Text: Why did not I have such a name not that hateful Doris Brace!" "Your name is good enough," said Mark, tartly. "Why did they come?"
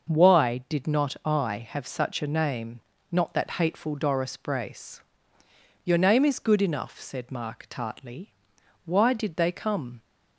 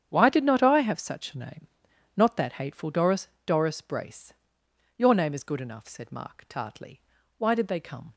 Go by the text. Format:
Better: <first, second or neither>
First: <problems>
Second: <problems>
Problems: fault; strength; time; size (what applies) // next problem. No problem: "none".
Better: first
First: pauses between "name" and "not"; slight; at 2.7 s; 0.32 s long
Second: starts louder than the rest; strong; until 1.1 s; 8.5 dB // pauses between "name" and "not"; noticeable; at 1.6 s; 0.48 s long // says "Doris" twice; at 3.4 s